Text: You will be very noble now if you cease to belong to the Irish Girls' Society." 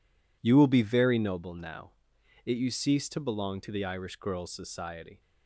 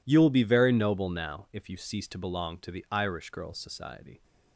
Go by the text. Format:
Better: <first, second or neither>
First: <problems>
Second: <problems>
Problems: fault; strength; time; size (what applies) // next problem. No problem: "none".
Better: second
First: says "it" for "if"; at 2.4 s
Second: none